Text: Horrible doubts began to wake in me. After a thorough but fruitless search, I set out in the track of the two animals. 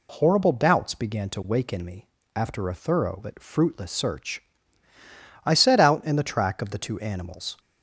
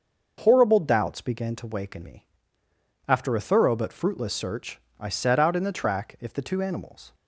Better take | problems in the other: first | starts louder than the rest; until 1.4 s; 6 dB // says "if" for "of"; at 6.2 s

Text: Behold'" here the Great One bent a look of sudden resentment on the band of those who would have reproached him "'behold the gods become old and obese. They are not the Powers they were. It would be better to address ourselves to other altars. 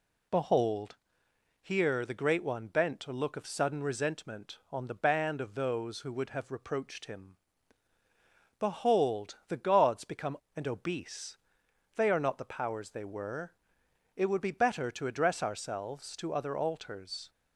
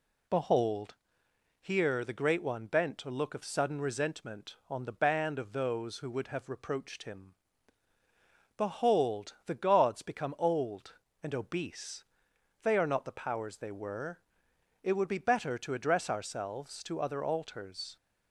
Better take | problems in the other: second | pauses between "Behold" and "here"; noticeable; at 0.9 s; 0.66 s long; noticeable in the second // pauses between "him" and "behold"; at 7.3 s; 1.2 s long; also in the second // skips "old"; at 10.4 s

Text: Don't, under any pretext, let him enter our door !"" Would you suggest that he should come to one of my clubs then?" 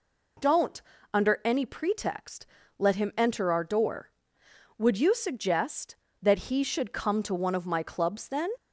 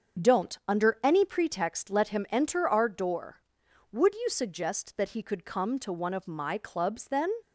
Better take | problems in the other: first | starts louder than the rest; until 1.3 s; 7 dB // says "could" for "should"; at 5.2 s

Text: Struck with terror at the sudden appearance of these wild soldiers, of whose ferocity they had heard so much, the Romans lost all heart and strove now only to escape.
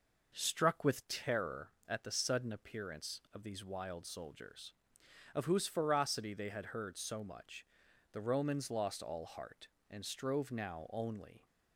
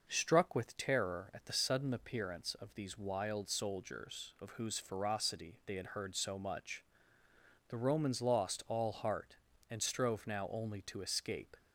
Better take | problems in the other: second | stops before "to escape"; at 11.4 s

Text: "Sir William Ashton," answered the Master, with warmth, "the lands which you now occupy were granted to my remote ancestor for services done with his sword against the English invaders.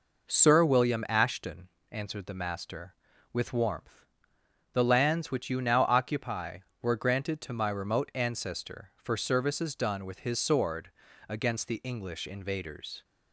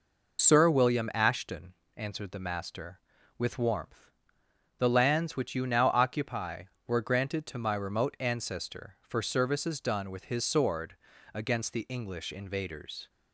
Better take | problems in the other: first | loses the start of "Sir"; at 0.3 s; 60 ms // pauses between "sword" and "against"; at 10.9 s; 0.38 s long; also in the first

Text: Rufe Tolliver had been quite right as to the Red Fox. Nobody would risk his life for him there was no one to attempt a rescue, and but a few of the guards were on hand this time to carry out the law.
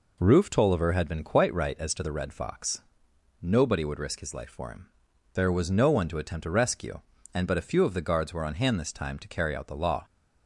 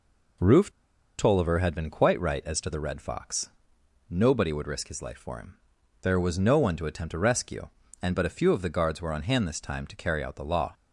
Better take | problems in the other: first | pauses between "Rufe" and "Tolliver"; noticeable; at 0.6 s; 0.49 s long // pauses between "him" and "there"; noticeable; at 5.5 s; 0.46 s long; noticeable in the first

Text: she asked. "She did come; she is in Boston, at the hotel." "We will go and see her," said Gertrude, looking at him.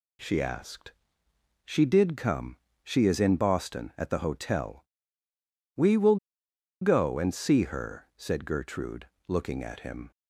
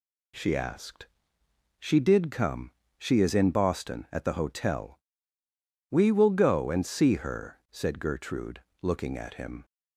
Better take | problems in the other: second | pauses between "will" and "go"; noticeable; at 6.1 s; 0.65 s long

